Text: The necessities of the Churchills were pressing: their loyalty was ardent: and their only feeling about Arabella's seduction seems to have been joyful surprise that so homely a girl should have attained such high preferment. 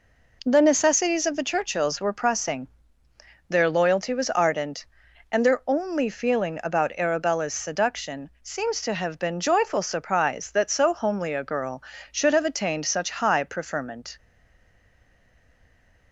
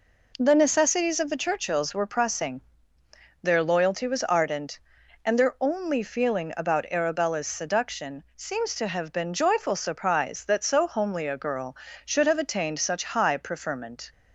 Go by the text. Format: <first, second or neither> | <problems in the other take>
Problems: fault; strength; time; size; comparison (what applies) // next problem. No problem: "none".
second | stays silent after the last word; noticeable; from 14.1 s on; 2.0 s long